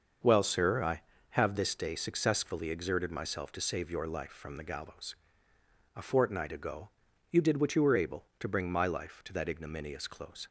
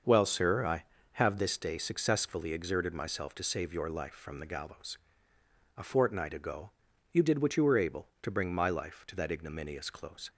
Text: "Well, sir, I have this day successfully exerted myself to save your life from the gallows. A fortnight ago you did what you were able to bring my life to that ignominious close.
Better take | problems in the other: neither | starts louder than the rest; the same in both // pauses between "ago" and "you"; the same in both

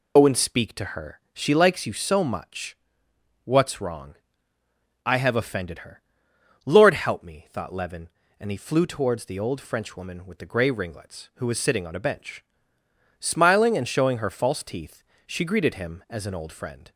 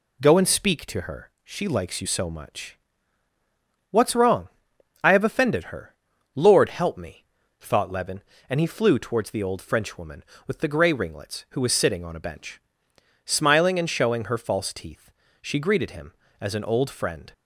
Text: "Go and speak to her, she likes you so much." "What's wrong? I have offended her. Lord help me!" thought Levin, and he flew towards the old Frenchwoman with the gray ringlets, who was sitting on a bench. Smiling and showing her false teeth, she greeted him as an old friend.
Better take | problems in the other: second | loses the start of "Go"; at 0.1 s; 90 ms

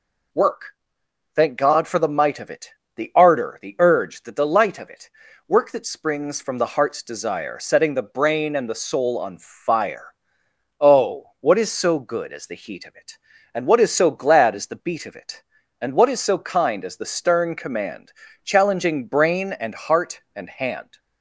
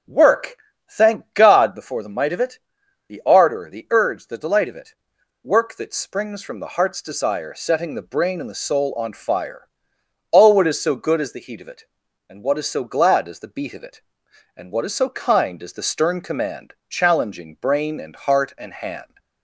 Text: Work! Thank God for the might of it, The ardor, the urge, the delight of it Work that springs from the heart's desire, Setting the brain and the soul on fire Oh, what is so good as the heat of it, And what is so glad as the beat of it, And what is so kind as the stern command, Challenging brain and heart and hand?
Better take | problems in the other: first | starts louder than the rest; strong; until 1.5 s; 9.5 dB // says "before" for "for"; at 1.7 s // pauses between "it" and "Work"; noticeable; at 4.9 s; 0.48 s long; also in the first // pauses between "fire" and "Oh"; noticeable; at 9.6 s; 0.66 s long; noticeable in the first

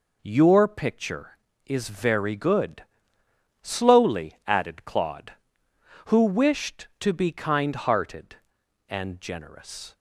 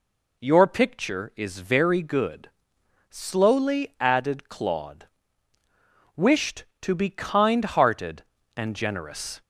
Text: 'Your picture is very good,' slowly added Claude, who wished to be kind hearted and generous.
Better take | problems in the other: first | skips "who"; at 5.6 s

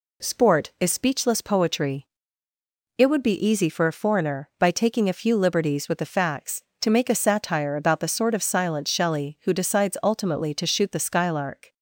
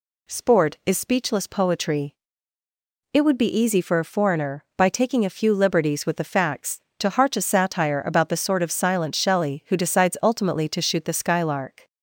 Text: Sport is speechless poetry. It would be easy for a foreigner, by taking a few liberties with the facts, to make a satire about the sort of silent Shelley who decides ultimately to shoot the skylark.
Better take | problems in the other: first | says "harch" for "make"; at 7.1 s

